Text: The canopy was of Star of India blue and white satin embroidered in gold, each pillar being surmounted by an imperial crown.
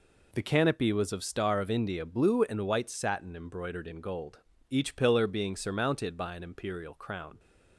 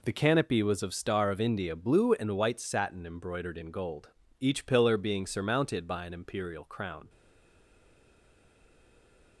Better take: first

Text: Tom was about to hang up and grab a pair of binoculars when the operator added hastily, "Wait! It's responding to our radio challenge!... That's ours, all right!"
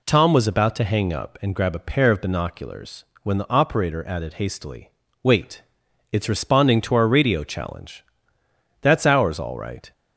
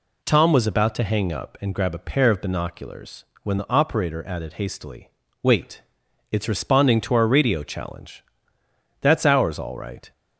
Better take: neither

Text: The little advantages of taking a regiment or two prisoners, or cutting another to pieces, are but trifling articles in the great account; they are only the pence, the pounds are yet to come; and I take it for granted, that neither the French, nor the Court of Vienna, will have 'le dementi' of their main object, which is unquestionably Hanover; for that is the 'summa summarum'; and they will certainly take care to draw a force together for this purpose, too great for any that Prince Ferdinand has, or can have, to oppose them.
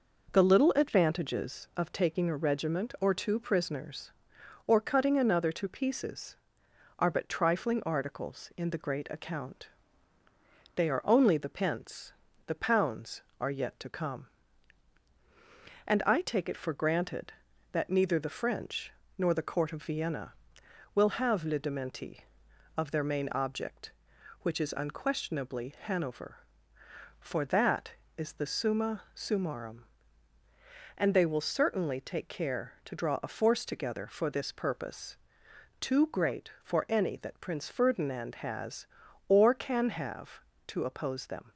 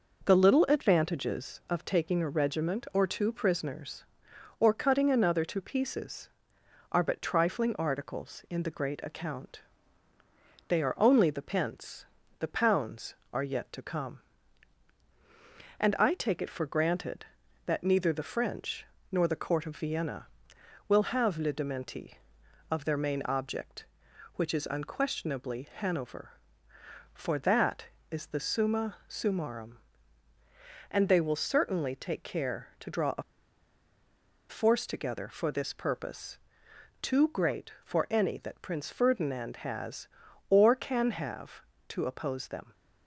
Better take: first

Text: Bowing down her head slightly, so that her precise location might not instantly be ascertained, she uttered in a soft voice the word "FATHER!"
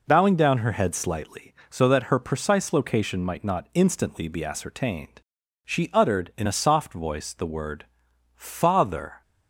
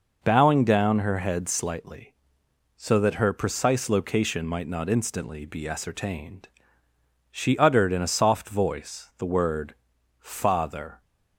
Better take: neither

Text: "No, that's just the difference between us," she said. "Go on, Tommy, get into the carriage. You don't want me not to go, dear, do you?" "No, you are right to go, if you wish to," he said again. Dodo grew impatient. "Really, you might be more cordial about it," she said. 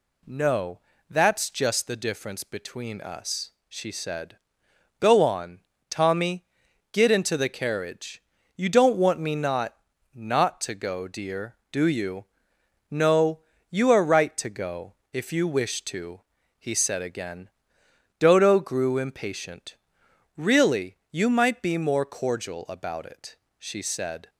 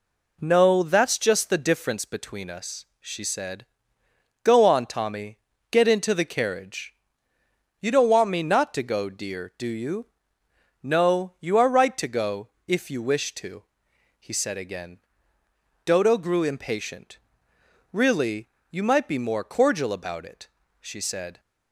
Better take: second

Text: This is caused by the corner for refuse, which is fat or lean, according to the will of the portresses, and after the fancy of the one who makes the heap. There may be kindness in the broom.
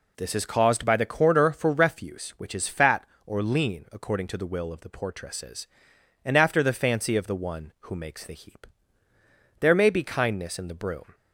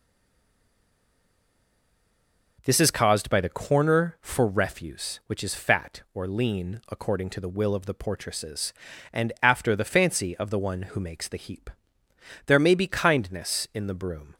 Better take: first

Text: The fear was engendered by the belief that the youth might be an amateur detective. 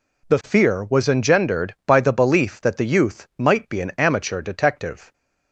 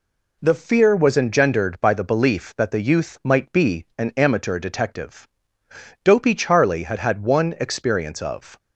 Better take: first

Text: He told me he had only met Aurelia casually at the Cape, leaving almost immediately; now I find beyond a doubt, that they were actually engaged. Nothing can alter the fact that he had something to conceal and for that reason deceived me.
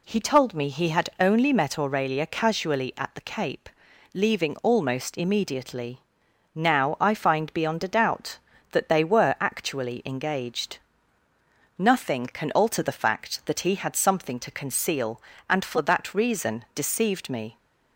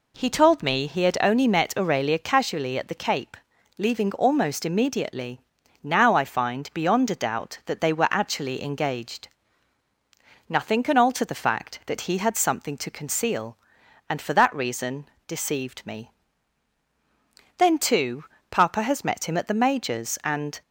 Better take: first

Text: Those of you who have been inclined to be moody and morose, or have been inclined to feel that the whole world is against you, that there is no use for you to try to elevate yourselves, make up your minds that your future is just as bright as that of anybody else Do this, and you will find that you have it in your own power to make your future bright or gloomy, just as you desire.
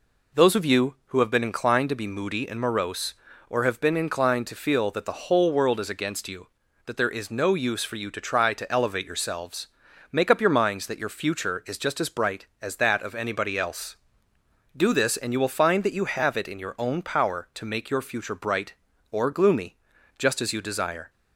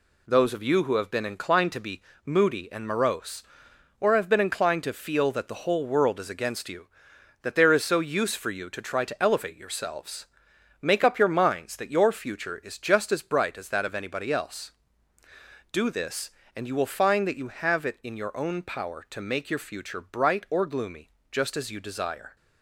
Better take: first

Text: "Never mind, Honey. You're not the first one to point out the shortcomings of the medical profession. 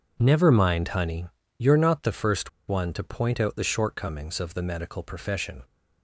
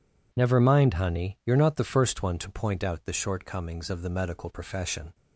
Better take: second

